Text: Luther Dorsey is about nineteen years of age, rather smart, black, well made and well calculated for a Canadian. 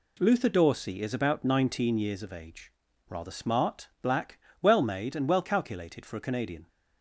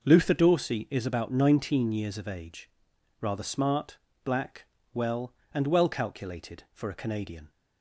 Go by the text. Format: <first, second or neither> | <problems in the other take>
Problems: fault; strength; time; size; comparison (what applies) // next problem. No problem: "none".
first | skips "made"; at 5.4 s